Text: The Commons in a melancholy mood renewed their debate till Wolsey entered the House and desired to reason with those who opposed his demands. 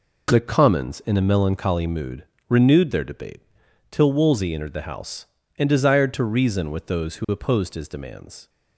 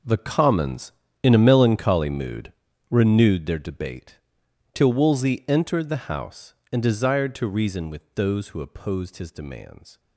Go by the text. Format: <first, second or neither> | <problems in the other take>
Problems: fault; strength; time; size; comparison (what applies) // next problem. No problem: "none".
first | gets quieter; strong; throughout; 14 dB // pauses between "mood" and "renewed"; at 2.5 s; 0.39 s long; slight in the first // pauses between "debate" and "till"; noticeable; at 4.1 s; 0.56 s long; noticeable in the first